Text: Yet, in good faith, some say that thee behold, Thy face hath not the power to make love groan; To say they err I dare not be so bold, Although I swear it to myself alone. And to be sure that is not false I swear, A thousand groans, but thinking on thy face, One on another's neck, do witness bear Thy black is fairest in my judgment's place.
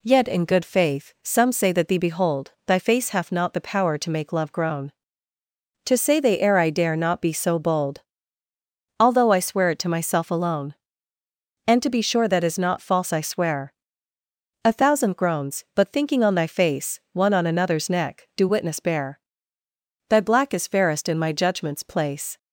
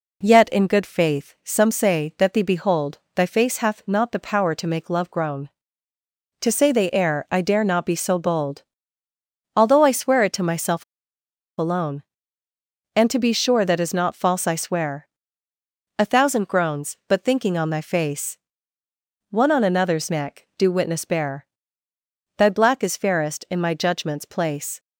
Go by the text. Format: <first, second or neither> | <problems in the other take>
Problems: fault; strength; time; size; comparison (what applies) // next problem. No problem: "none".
first | pauses between "myself" and "alone"; noticeable; at 10.8 s; 0.75 s long // pauses between "bear" and "Thy"; noticeable; at 21.4 s; 0.92 s long; noticeable in the first